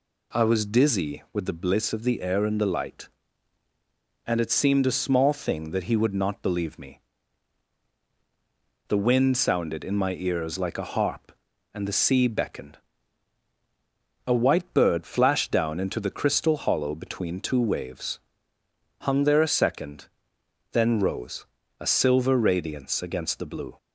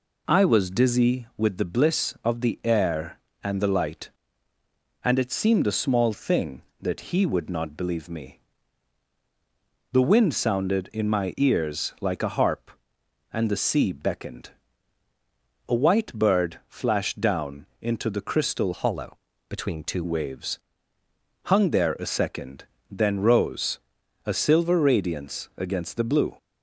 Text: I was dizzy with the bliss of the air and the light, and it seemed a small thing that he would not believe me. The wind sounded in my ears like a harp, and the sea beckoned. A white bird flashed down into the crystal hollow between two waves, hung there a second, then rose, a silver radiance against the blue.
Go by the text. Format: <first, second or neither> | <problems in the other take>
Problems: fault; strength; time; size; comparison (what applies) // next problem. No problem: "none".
first | pauses between "down" and "into"; slight; at 17.6 s; 0.16 s long // changes voice from "hollow" to "two"; from 18.7 to 20.0 s; 1.3 s long // pauses between "hollow" and "between"; slight; at 19.1 s; 0.32 s long